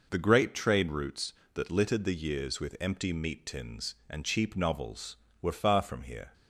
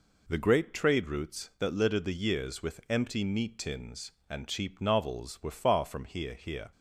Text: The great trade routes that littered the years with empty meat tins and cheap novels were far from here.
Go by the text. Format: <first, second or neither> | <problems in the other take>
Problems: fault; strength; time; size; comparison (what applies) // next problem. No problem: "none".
first | says "here" twice; at 6.3 s